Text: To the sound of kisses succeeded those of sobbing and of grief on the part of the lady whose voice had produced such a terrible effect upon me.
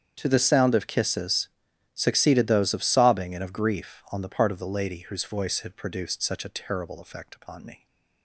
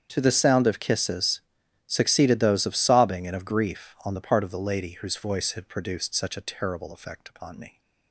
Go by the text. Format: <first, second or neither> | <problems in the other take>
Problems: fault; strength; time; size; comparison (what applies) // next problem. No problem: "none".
neither | starts louder than the rest; strong; the same in both // pauses between "kisses" and "succeeded"; noticeable; the same in both